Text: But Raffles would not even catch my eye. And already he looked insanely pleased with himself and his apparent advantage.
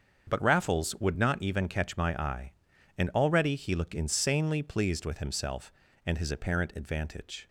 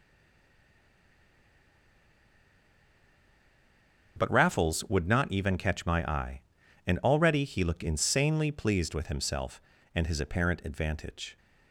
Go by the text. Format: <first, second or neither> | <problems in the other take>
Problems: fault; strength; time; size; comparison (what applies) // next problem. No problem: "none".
first | stays silent before the first word; strong; until 4.1 s; 4.1 s long // starts louder than the rest; until 5.1 s; 6.5 dB; also in the first